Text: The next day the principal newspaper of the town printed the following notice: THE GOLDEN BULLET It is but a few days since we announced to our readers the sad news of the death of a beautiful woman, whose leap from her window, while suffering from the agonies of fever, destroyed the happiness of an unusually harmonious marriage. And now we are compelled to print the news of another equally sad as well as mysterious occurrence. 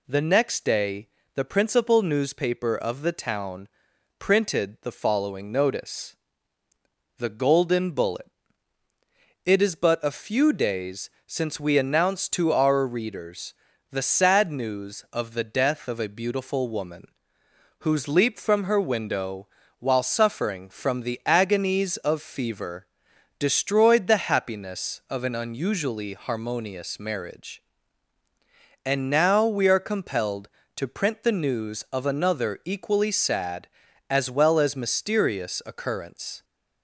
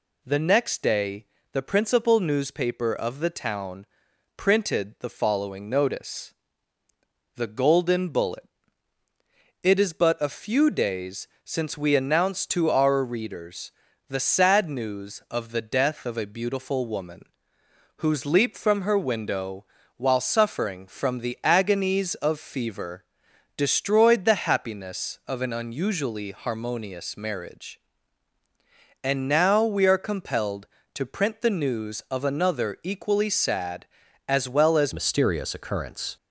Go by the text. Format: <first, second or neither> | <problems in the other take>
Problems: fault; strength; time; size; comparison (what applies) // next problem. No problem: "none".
first | pauses between "day" and "the"; slight; at 1.2 s; 0.26 s long; slight in the first // pauses between "town" and "printed"; noticeable; at 3.8 s; 0.50 s long; noticeable in the first // pauses between "BULLET" and "It"; at 8.4 s; 1.2 s long; also in the first // pauses between "days" and "since"; slight; at 11.2 s; 0.18 s long; slight in the first // pauses between "readers" and "the"; slight; at 13.7 s; 0.36 s long; slight in the first // changes voice at "mysterious"; from 34.9 s on; 1.2 s long